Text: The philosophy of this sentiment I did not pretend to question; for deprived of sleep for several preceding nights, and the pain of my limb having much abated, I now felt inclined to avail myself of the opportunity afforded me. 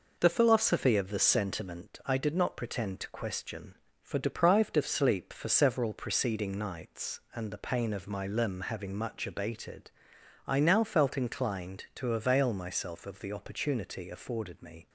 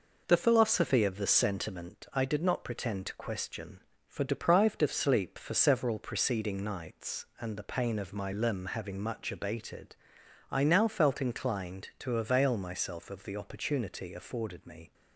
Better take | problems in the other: neither | none

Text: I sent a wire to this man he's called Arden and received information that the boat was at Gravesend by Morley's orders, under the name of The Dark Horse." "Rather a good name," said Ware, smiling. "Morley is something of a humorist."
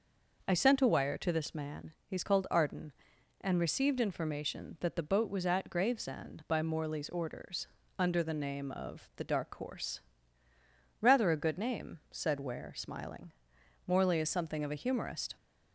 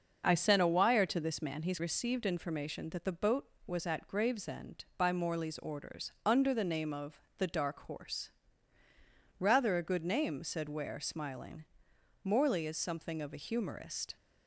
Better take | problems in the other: first | starts louder than the rest; noticeable; until 1.2 s; 6 dB // skips "called Arden and"; at 1.7 s // pauses between "of" and "The"; slight; at 7.1 s; 0.20 s long

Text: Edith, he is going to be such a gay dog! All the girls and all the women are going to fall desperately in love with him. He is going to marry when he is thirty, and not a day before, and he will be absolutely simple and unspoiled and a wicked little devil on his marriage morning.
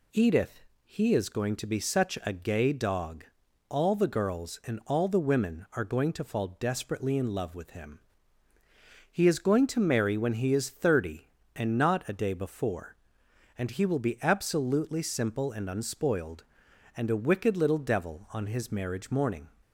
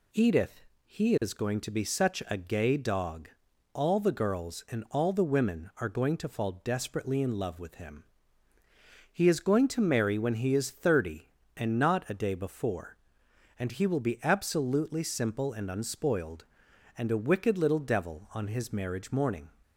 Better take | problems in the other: neither | none

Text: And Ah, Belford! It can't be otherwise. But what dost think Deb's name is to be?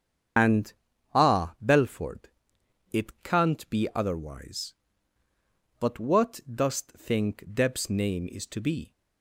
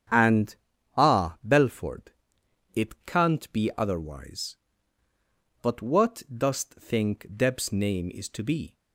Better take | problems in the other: second | loses the start of "And"; at 0.3 s; 105 ms // starts louder than the rest; strong; until 1.8 s; 7.5 dB; strong in the second // pauses between "And" and "Ah"; at 0.7 s; 0.42 s long; also in the second

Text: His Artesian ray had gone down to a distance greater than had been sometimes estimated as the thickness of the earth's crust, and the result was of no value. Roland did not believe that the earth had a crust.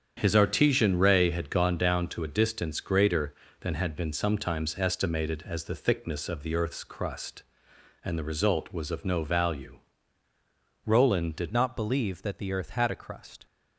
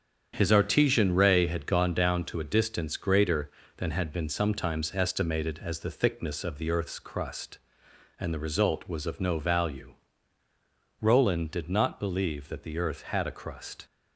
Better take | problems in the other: second | starts louder than the rest; strong; until 1.1 s; 8 dB; strong in the second // changes voice at "not"; from 11.5 s on; 1.9 s long

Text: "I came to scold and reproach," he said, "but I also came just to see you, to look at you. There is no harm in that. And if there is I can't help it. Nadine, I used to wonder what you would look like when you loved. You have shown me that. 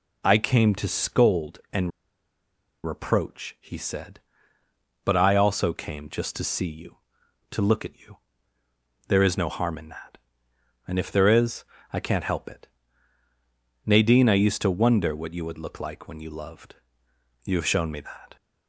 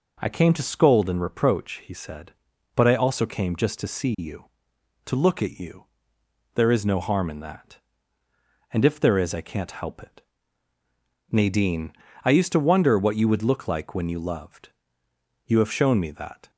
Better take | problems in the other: second | pauses between "and" and "reproach"; noticeable; at 1.9 s; 0.95 s long // pauses between "is" and "I"; slight; at 11.6 s; 0.30 s long

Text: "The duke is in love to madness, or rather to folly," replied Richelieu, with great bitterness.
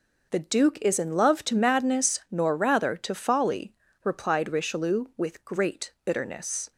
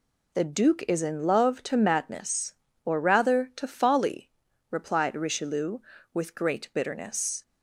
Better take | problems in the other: second | says "nor" for "or"; at 2.3 s

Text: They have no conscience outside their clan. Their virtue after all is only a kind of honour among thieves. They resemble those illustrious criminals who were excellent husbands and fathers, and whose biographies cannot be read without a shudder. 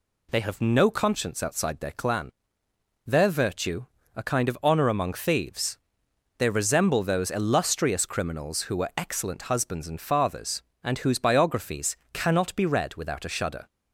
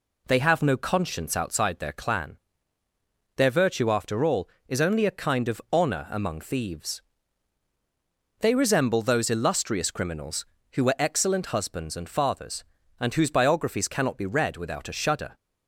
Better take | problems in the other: second | skips "after all is only"; at 4.0 s // pauses between "biographies" and "cannot"; slight; at 11.9 s; 0.18 s long

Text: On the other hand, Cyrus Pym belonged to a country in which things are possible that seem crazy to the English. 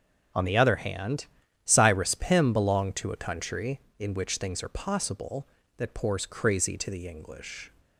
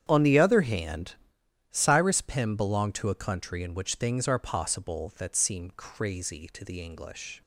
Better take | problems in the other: second | starts louder than the rest; strong; until 1.7 s; 8 dB; strong in the second // says "pours" for "seem"; at 5.9 s

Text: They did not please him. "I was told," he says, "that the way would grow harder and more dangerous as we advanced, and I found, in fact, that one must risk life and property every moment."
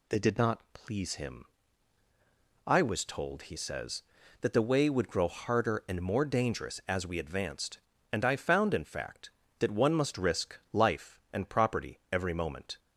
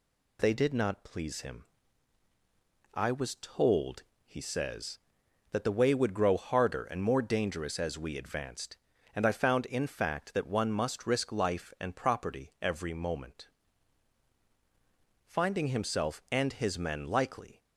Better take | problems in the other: first | goes on to say "Finding himself and his men likely"; strong; from 15.2 s on; 2.3 s long

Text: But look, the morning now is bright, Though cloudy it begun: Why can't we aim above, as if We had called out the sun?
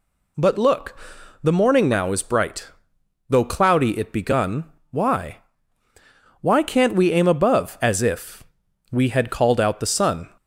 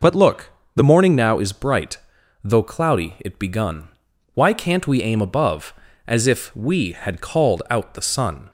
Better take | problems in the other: second | says "Why" twice; at 6.4 s // pauses between "if" and "We"; noticeable; at 8.4 s; 0.48 s long

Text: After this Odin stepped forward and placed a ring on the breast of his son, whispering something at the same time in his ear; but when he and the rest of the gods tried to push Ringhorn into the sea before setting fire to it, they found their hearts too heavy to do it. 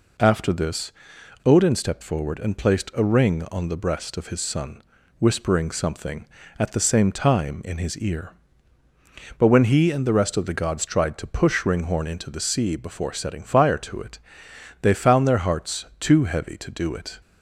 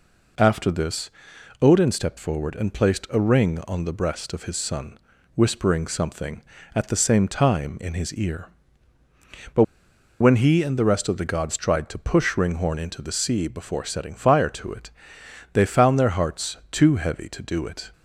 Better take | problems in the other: first | pauses between "this" and "Odin"; noticeable; at 1.1 s; 0.52 s long; noticeable in the first // pauses between "but" and "when"; noticeable; at 9.6 s; 0.58 s long // pauses between "hearts" and "too"; slight; at 16.5 s; 0.16 s long; slight in the first

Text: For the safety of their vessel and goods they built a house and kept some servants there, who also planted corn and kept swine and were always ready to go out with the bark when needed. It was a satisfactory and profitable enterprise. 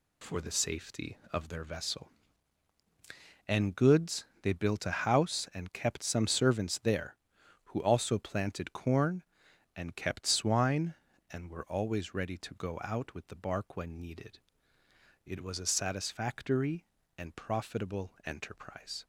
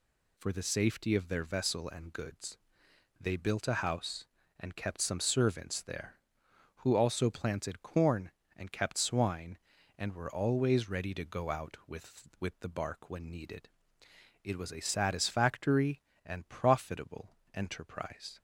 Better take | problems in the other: first | pauses between "goods" and "they"; noticeable; at 2.5 s; 0.60 s long; slight in the first // says "with" twice; at 12.3 s // pauses between "profitable" and "enterprise"; slight; at 17.3 s; 0.24 s long

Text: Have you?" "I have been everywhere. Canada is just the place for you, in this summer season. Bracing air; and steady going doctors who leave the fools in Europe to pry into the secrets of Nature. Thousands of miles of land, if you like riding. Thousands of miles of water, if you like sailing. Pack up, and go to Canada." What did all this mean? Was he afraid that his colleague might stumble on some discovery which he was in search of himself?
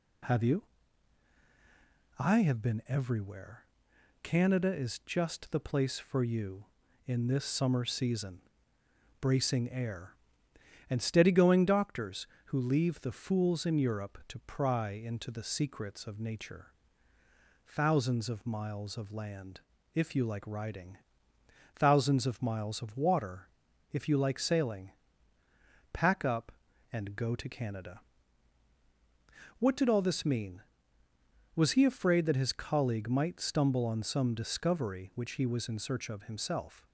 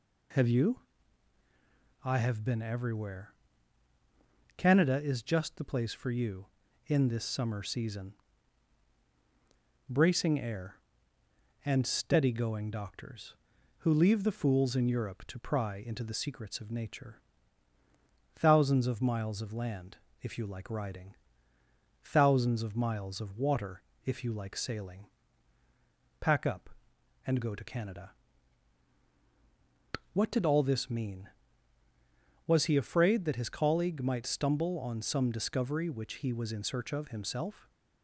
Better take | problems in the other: neither | none

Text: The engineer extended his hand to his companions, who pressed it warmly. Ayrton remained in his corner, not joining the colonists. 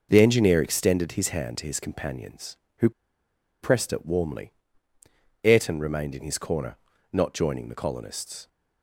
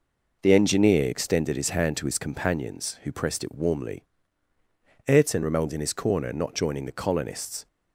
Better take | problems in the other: second | pauses between "who" and "pressed"; noticeable; at 2.8 s; 0.72 s long

